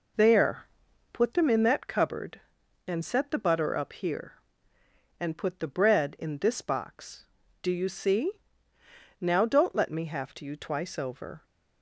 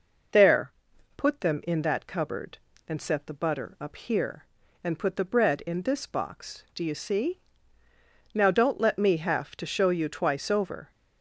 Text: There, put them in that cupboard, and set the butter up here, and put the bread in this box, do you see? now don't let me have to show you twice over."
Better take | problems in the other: second | skips "show"; at 10.4 s

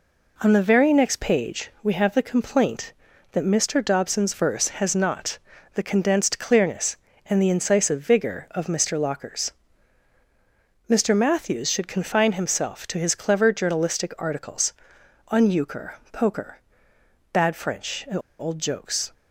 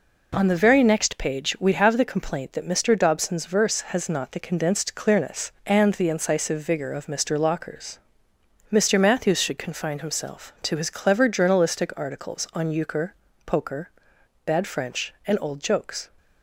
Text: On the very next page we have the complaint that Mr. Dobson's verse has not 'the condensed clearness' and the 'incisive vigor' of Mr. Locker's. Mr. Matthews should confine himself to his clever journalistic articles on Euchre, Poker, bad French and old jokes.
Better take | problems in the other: second | pauses between "not" and "the"; slight; at 5.3 s; 0.36 s long // pauses between "and" and "old"; slight; at 18.1 s; 0.20 s long

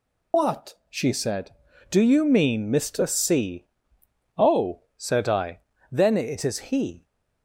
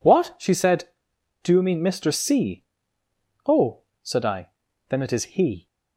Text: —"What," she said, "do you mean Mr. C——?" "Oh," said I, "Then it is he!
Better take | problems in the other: second | loses the start of "What"; at 0.3 s; 80 ms

